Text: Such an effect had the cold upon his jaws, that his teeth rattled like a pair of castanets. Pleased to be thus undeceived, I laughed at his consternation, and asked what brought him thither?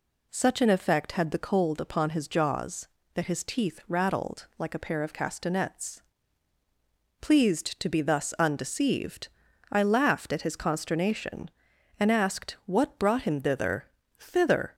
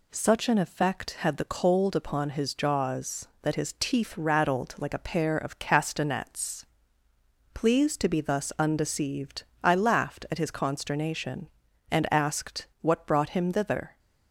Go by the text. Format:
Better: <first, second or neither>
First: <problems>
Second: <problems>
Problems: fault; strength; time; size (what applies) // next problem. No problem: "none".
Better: second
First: says "thither" twice; at 14.1 s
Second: none